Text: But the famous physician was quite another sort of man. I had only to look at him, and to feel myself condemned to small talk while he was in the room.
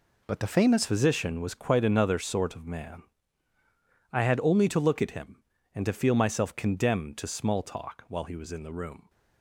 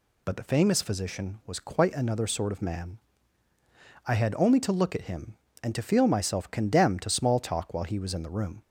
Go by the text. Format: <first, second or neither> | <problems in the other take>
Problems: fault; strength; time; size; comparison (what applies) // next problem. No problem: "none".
second | changes voice at "physician"; from 0.8 s on; 8.2 s long